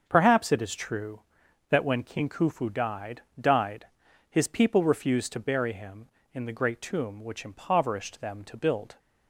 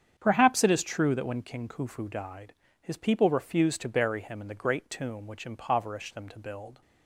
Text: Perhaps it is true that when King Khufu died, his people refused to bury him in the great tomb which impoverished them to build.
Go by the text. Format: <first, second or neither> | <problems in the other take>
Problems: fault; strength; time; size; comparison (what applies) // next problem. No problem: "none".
second | starts louder than the rest; until 1.0 s; 6.5 dB; strong in the second // says "died" twice; at 3.3 s